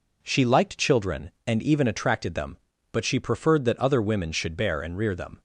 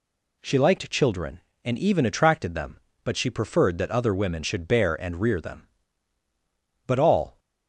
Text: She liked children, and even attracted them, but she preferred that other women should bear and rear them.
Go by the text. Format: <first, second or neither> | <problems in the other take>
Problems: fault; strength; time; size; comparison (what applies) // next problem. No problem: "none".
first | goes on to say "But all"; from 6.8 s on; 0.52 s long